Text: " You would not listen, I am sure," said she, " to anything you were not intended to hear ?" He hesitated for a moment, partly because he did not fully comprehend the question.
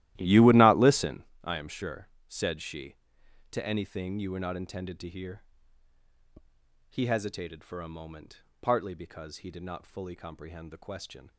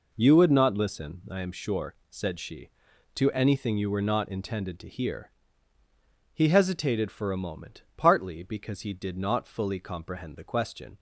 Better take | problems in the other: second | starts louder than the rest; strong; until 1.4 s; 14.5 dB

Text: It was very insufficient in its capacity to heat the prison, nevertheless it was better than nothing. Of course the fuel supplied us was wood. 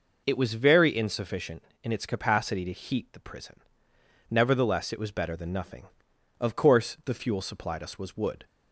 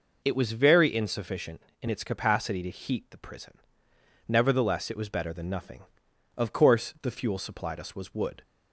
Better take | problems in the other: neither | none

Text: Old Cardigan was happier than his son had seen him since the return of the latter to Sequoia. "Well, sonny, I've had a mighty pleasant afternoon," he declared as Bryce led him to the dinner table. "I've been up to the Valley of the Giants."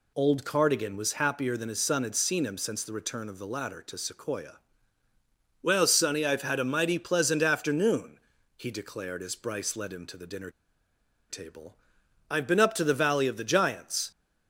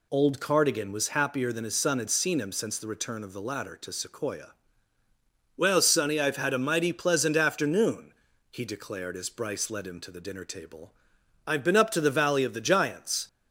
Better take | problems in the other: second | pauses between "dinner" and "table"; noticeable; at 10.5 s; 0.78 s long

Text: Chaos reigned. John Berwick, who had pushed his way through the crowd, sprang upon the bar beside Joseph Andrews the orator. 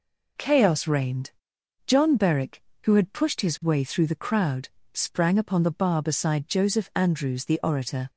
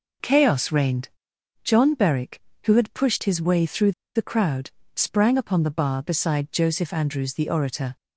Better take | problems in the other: first | pauses between "through" and "the"; slight; at 3.9 s; 0.23 s long

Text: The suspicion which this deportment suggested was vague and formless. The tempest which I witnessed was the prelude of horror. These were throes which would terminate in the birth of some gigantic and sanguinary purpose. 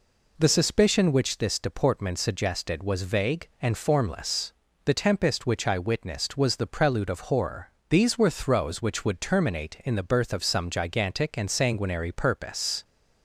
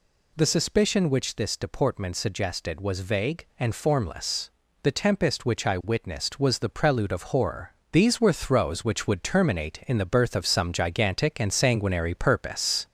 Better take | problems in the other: first | gets louder; slight; throughout; 3 dB

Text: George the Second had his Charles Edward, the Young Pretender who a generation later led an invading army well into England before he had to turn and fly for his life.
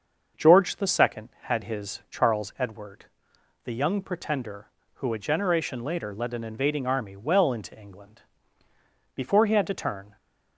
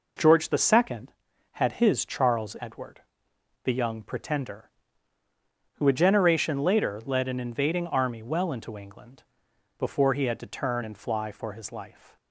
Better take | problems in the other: second | starts louder than the rest; until 1.5 s; 6.5 dB // pauses between "England" and "before"; noticeable; at 8.2 s; 0.92 s long; noticeable in the second // stops before "and fly for his life"; at 10.1 s

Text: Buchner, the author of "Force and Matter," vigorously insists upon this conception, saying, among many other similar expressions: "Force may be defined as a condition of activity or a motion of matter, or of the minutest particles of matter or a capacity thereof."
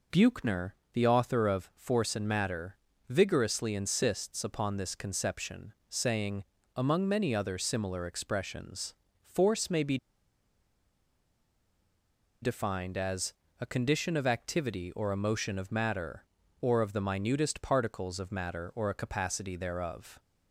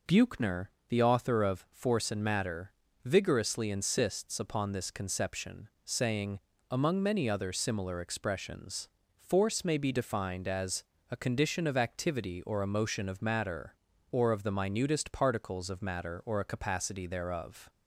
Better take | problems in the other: second | pauses between "be" and "defined"; strong; at 9.9 s; 2.4 s long // pauses between "as" and "a"; slight; at 13.3 s; 0.26 s long; slight in the second

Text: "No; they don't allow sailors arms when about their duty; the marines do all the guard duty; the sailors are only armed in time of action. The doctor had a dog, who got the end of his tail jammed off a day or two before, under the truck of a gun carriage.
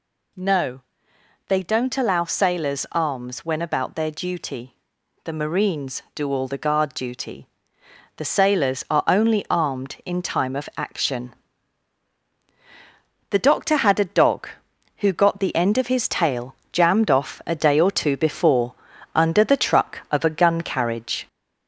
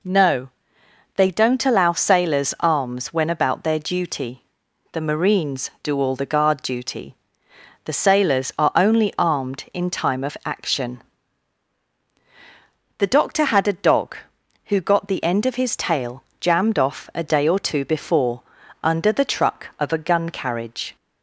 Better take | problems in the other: second | gets louder; slight; throughout; 3 dB // pauses between "tail" and "jammed"; slight; at 16.5 s; 0.16 s long; slight in the second

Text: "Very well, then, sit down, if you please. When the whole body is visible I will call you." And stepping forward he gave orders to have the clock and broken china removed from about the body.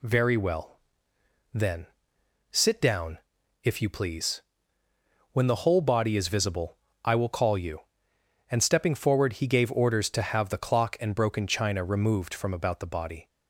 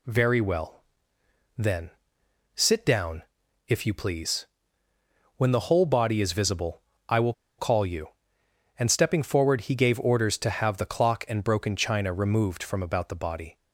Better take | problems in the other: first | pauses between "visible" and "I"; slight; at 6.8 s; 0.28 s long; slight in the first // pauses between "will" and "call"; slight; at 7.3 s; 0.25 s long

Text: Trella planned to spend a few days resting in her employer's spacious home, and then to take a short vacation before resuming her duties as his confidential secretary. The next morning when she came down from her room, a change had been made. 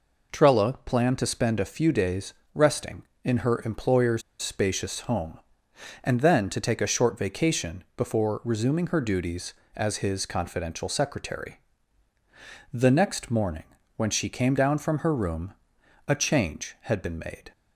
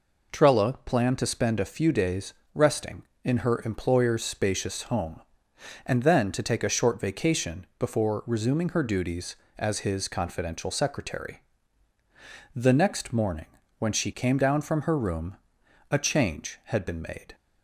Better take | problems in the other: second | pauses between "days" and "resting"; slight; at 2.3 s; 0.20 s long; slight in the second // pauses between "employer's" and "spacious"; slight; at 4.2 s; 0.19 s long // pauses between "morning" and "when"; slight; at 13.6 s; 0.32 s long; slight in the second

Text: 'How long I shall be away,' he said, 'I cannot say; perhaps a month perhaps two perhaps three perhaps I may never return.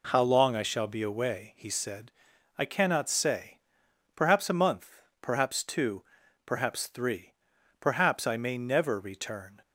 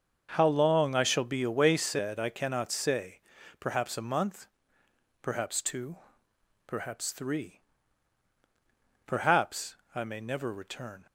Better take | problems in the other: first | starts louder than the rest; until 1.3 s; 6.5 dB // skips "he"; at 1.7 s // pauses between "month" and "perhaps"; noticeable; at 4.4 s; 0.76 s long; slight in the first // pauses between "two" and "perhaps"; noticeable; at 5.9 s; 0.70 s long; also in the first // pauses between "three" and "perhaps"; strong; at 7.6 s; 1.4 s long; also in the first // pauses between "perhaps" and "I"; slight; at 9.7 s; 0.20 s long

